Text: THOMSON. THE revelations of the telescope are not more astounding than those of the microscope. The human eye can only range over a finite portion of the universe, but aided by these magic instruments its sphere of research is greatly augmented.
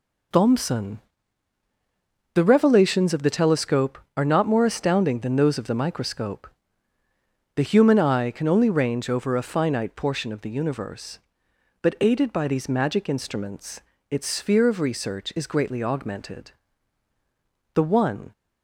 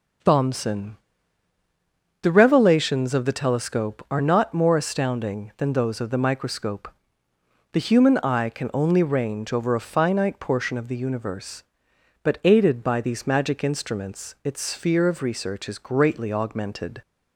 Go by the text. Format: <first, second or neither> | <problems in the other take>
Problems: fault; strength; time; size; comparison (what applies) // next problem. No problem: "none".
second | pauses between "instruments" and "its"; slight; at 13.8 s; 0.28 s long // goes on to say "The one"; from 17.7 s on; 0.58 s long